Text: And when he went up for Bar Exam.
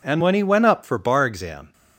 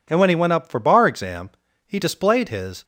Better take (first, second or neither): first